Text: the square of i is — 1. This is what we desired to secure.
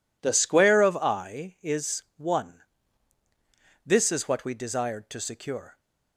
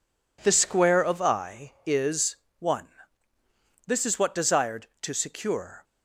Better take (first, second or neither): first